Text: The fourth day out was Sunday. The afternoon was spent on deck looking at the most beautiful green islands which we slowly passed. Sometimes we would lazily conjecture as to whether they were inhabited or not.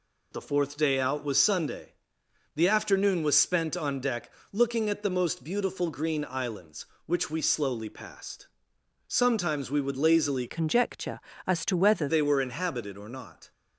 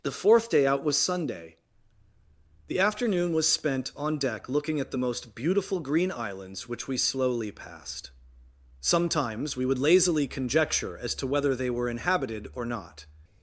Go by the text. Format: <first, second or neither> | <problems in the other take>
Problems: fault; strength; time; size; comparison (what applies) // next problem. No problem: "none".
second | pauses between "deck" and "looking"; slight; at 4.3 s; 0.20 s long // changes voice from "conjecture" to "whether"; from 10.4 to 12.0 s; 1.6 s long